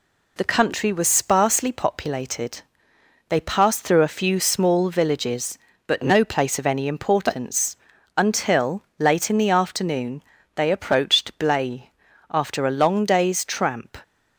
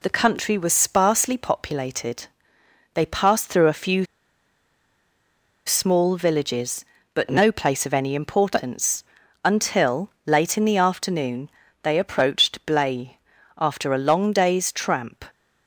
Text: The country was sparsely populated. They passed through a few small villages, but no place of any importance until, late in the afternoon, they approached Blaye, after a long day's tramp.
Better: first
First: pauses between "importance" and "until"; at 7.7 s; 0.40 s long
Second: pauses between "few" and "small"; strong; at 4.0 s; 1.6 s long // pauses between "importance" and "until"; at 9.0 s; 0.40 s long

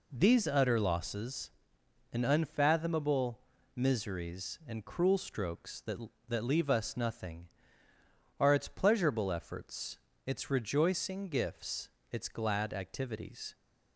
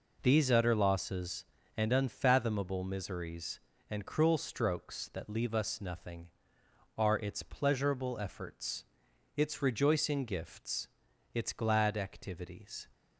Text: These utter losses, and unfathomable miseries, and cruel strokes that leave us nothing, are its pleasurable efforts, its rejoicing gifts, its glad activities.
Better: second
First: pauses between "unfathomable" and "miseries"; at 3.3 s; 0.38 s long // says "that" twice; at 6.2 s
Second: none

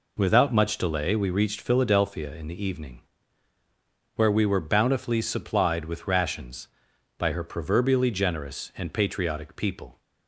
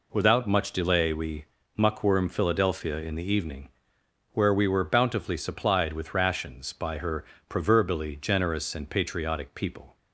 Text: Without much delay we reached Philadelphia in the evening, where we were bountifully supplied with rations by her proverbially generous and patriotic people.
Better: first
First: none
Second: says "muckworm" for "reached"; at 1.7 s // pauses between "her" and "proverbially"; slight; at 7.2 s; 0.24 s long

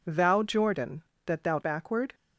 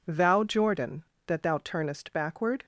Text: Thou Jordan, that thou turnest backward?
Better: second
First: skips "turnest"; at 1.6 s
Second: none

